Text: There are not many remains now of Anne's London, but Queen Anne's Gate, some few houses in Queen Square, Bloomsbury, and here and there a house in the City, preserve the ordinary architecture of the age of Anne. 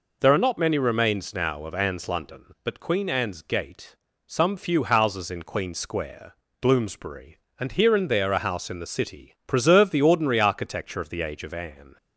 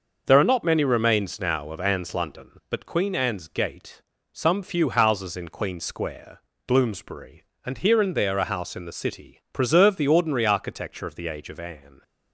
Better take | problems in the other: first | gets quieter; throughout; 6.5 dB

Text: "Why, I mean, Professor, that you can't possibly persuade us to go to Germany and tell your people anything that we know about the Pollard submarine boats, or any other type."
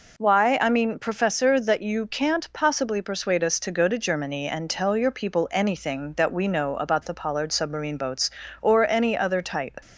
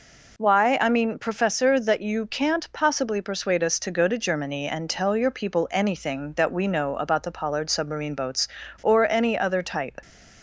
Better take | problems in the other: neither | none

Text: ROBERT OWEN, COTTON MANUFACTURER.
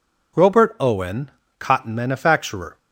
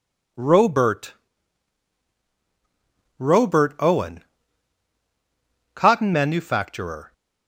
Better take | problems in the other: first | says "ROBERT" twice; at 3.1 s

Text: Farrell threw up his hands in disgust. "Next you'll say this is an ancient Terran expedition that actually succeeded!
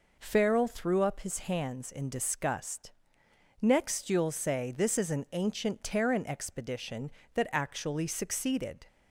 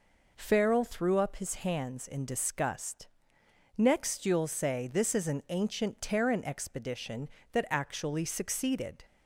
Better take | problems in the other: neither | none

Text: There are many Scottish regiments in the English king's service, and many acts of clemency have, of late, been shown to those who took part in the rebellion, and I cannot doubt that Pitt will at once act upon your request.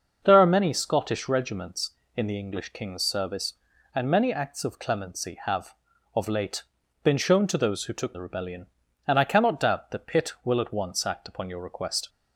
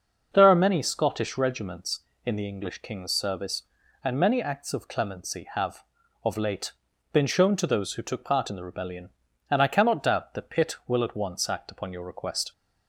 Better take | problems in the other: second | starts louder than the rest; until 1.2 s; 6 dB // skips "part in"; at 8.1 s

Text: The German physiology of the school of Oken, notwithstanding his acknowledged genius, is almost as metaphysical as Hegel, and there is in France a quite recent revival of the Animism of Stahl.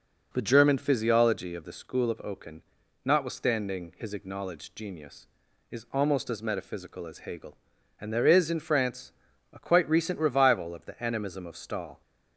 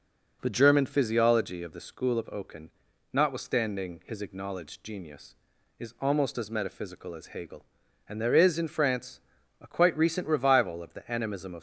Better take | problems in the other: first | pauses between "France" and "a"; at 9.1 s; 0.40 s long; also in the first // stops before "Stahl"; at 11.5 s

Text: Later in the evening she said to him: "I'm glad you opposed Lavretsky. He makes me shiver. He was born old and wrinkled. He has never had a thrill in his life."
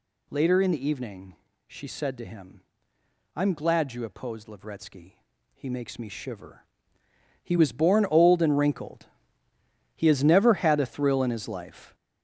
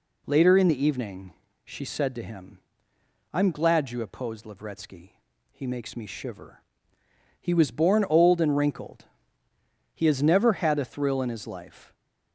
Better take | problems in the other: second | gets louder; throughout; 7 dB // pauses between "evening" and "she"; slight; at 1.3 s; 0.32 s long; slight in the second

